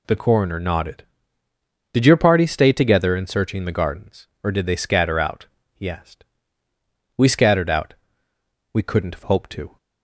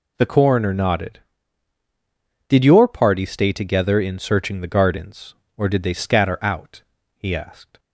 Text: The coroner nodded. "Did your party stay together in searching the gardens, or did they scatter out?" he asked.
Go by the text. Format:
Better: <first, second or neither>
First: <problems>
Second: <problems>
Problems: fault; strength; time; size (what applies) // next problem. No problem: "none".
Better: second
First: goes on to say "We scattered out We couldn't have hoped to"; strong; from 7.1 s on; 2.6 s long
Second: none